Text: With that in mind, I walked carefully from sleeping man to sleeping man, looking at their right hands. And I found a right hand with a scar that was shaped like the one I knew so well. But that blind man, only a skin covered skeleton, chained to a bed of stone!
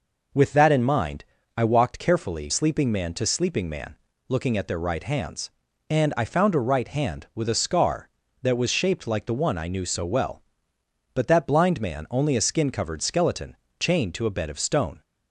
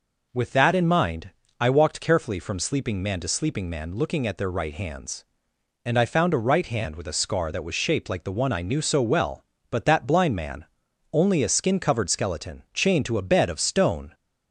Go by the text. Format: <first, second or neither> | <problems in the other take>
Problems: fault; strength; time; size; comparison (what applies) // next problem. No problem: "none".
second | skips "from"; at 2.4 s